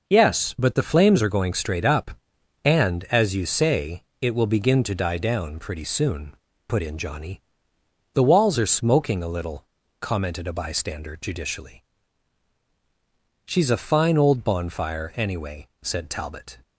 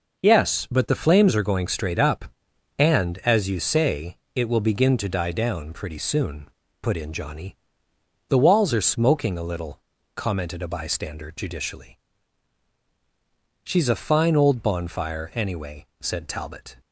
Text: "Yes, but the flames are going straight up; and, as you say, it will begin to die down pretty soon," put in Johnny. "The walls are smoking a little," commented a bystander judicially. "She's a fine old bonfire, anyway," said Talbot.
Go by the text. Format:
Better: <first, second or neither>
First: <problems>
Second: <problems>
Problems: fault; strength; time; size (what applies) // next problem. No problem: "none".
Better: neither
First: none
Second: none